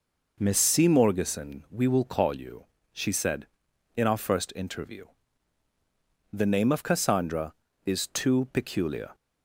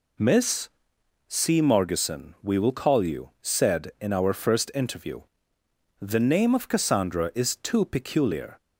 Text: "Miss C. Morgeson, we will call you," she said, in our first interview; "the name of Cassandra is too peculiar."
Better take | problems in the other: first | pauses between "Miss" and "C"; noticeable; at 0.6 s; 0.58 s long // skips "she"; at 3.3 s

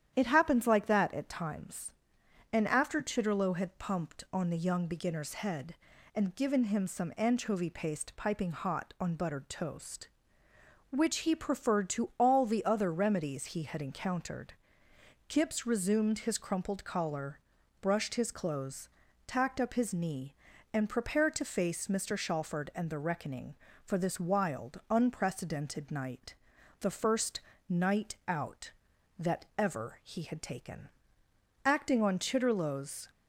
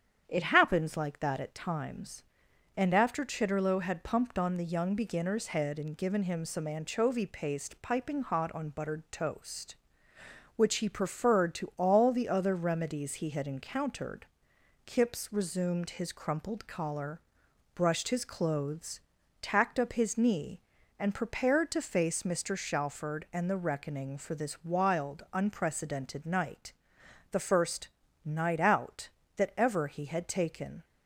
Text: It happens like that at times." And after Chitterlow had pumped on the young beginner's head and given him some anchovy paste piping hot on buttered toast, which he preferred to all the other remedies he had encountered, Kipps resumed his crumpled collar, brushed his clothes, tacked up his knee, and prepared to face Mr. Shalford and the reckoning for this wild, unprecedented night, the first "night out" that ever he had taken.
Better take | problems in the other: second | starts louder than the rest; strong; until 1.1 s; 10 dB; strong in the second // pauses between "first" and "night"; slight; at 27.4 s; 0.26 s long; slight in the second // goes on to say "Acting on Chitterlow's"; from 31.6 s on; 1.4 s long

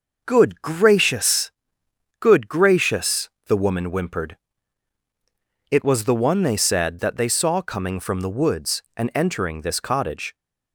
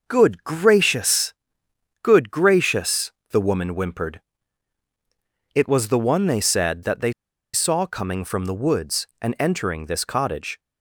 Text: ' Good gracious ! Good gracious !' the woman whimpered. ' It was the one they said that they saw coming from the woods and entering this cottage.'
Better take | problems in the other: first | pauses between "they" and "saw"; at 7.1 s; 0.41 s long

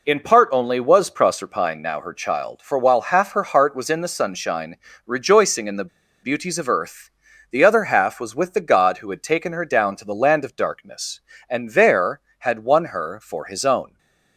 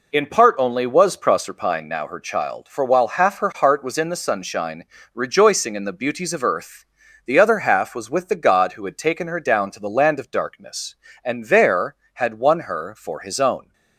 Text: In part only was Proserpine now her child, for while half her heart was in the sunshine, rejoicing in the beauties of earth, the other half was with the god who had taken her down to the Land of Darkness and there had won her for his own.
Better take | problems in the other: second | pauses between "the" and "beauties"; slight; at 5.8 s; 0.34 s long // stays silent after the last word; slight; from 13.8 s on; 0.5 s long

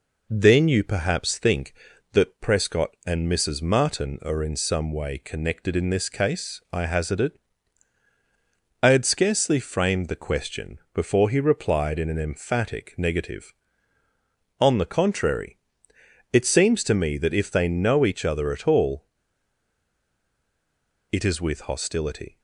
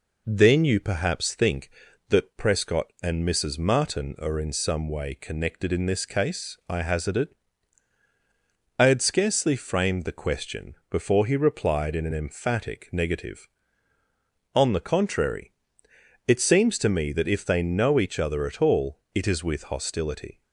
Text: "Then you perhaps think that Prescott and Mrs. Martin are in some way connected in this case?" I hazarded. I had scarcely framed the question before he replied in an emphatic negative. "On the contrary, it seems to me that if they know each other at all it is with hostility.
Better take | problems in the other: second | pauses between "all" and "it"; strong; at 19.0 s; 2.0 s long

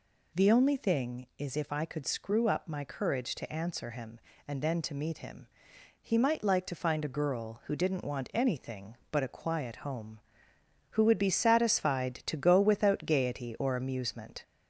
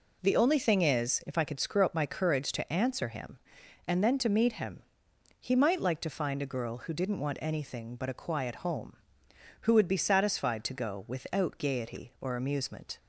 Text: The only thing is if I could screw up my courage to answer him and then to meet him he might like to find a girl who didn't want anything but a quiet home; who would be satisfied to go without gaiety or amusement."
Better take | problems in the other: second | gets louder; slight; throughout; 3 dB // pauses between "him" and "he"; noticeable; at 5.4 s; 0.58 s long; noticeable in the second

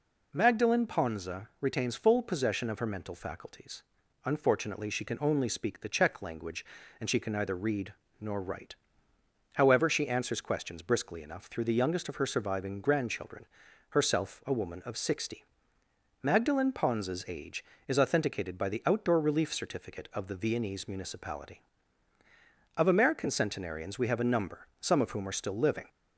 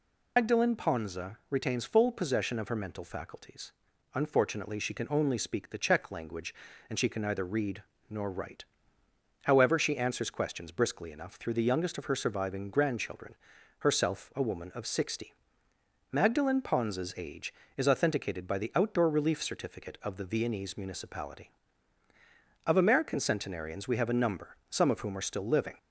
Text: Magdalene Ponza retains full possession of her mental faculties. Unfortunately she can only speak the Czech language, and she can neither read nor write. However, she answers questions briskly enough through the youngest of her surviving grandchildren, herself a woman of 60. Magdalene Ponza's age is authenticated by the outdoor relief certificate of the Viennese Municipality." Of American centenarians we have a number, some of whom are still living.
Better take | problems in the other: first | loses the start of "Magdalene"; at 0.3 s; 140 ms // pauses between "read" and "nor"; slight; at 7.8 s; 0.26 s long; slight in the first

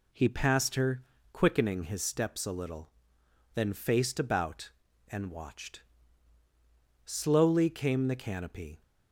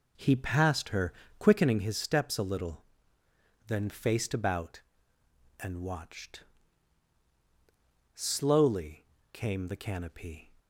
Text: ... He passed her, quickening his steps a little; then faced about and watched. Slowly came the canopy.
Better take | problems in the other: first | starts louder than the rest; noticeable; until 1.9 s; 4 dB // pauses between "Slowly" and "came"; slight; at 9.0 s; 0.30 s long

